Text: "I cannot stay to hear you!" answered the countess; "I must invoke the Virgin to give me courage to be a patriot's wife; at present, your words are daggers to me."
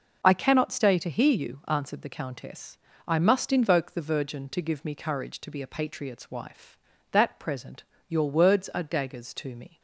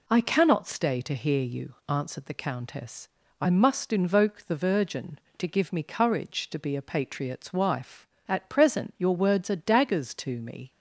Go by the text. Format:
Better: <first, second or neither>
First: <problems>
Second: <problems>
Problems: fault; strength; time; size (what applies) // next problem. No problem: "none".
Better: second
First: says "that" for "at"; at 7.0 s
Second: none